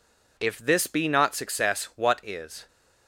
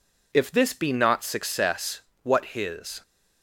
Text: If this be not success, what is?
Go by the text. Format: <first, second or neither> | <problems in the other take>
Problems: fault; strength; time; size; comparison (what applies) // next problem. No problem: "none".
first | says "his" for "is"; at 2.5 s